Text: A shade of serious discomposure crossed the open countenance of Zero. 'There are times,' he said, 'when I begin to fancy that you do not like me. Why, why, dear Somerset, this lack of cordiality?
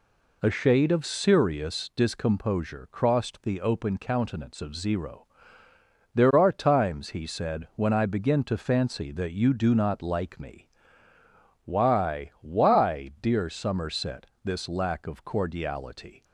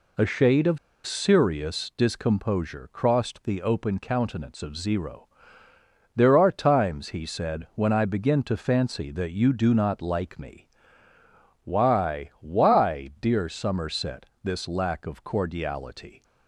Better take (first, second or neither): first